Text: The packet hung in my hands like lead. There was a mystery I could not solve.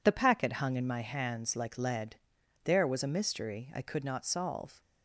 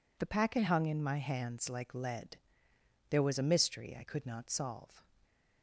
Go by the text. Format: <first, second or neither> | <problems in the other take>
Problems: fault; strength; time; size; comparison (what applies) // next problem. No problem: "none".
neither | none